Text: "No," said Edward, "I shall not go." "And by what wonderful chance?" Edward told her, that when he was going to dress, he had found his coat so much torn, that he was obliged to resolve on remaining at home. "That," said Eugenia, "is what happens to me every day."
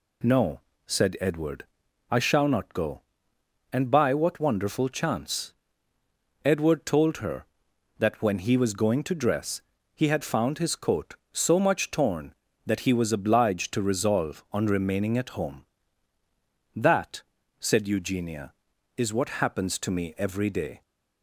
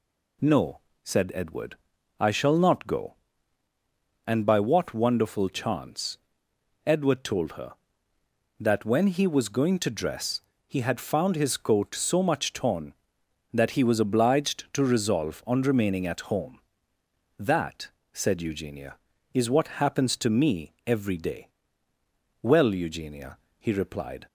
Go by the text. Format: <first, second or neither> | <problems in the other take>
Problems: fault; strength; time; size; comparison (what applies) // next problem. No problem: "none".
first | goes on to say "Well Eugenia he replied"; strong; from 22.4 s on; 1.8 s long